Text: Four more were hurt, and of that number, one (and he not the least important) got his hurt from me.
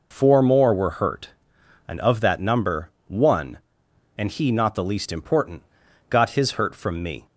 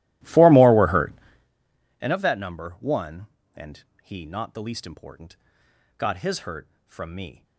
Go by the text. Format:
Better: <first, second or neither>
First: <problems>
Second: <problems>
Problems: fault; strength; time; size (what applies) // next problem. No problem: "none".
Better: first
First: none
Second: starts louder than the rest; strong; until 1.5 s; 16 dB // pauses between "and" and "he"; slight; at 3.8 s; 0.20 s long